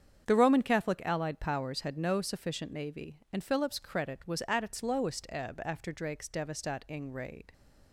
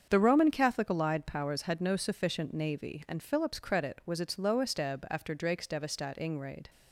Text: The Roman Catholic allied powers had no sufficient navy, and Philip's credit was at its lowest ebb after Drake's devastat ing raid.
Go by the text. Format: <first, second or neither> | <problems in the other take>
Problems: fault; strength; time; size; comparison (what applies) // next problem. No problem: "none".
first | starts louder than the rest; strong; until 1.1 s; 7 dB; strong in the first // skips "at"; at 4.1 s